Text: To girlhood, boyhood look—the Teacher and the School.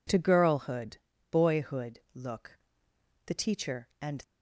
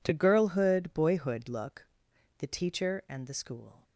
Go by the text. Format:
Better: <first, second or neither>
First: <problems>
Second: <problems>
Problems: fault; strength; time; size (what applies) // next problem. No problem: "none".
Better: second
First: stops before "the School"; at 4.2 s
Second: none